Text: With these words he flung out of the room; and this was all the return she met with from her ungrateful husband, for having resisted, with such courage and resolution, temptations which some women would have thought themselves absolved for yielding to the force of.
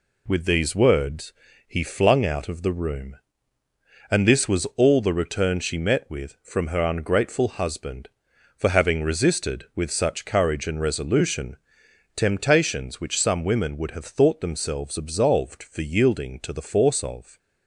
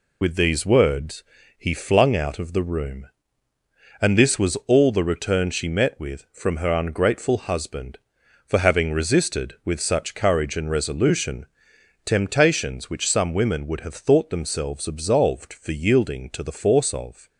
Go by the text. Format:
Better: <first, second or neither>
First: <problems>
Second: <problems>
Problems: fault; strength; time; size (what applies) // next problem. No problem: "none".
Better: first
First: pauses between "words" and "he"; slight; at 1.3 s; 0.34 s long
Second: loses the start of "With"; at 0.2 s; 50 ms // pauses between "words" and "he"; slight; at 1.2 s; 0.34 s long